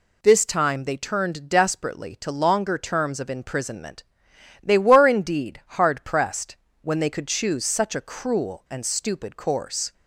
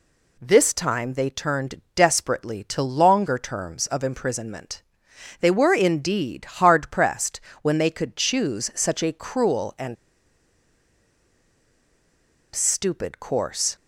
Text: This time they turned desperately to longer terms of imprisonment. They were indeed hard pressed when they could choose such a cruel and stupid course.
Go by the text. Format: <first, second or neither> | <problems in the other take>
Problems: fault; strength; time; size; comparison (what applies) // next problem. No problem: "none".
first | pauses between "pressed" and "when"; slight; at 7.3 s; 0.24 s long; slight in the first // pauses between "and" and "stupid"; strong; at 9.9 s; 2.5 s long